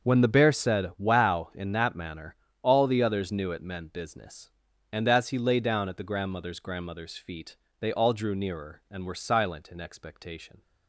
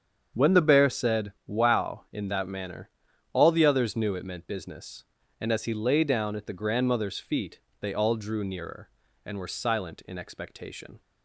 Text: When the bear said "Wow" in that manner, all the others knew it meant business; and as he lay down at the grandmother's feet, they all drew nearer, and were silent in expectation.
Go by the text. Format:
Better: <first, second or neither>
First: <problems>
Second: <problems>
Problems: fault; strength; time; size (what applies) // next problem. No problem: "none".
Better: second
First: starts louder than the rest; until 1.1 s; 6.5 dB // says "grandmother's" twice; at 6.5 s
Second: starts louder than the rest; strong; until 1.4 s; 7.5 dB